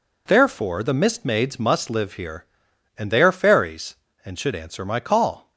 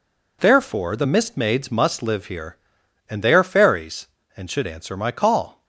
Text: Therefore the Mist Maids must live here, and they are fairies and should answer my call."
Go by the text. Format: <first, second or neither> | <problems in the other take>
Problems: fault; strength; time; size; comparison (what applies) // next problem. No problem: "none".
neither | none